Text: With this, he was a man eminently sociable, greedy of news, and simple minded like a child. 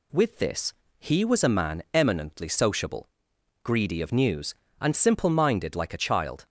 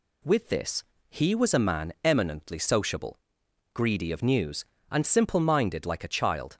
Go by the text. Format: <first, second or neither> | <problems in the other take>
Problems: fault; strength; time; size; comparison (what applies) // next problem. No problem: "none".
neither | none